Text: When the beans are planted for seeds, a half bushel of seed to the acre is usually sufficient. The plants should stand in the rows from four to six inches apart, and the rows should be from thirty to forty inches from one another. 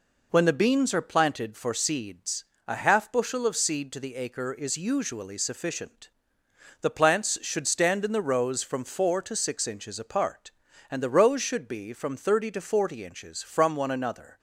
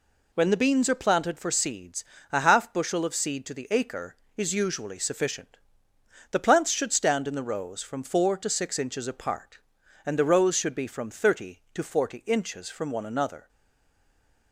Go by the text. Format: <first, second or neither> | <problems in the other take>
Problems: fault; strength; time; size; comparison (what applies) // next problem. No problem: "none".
first | stays silent after the last word; from 13.4 s on; 1.1 s long